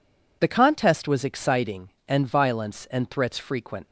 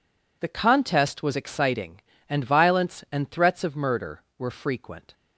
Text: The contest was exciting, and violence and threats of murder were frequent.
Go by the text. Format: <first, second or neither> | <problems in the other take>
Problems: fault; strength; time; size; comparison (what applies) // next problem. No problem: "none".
second | skips "of murder were"; at 3.3 s